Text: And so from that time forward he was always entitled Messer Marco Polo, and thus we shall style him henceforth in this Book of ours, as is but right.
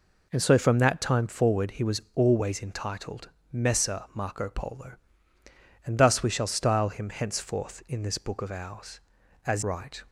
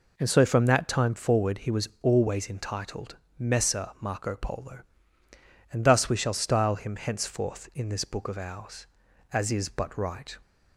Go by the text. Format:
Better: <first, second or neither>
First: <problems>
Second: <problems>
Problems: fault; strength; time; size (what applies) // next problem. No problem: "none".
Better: second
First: pauses between "entitled" and "Messer"; slight; at 3.2 s; 0.22 s long // skips "is but"; at 9.6 s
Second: pauses between "entitled" and "Messer"; slight; at 3.1 s; 0.21 s long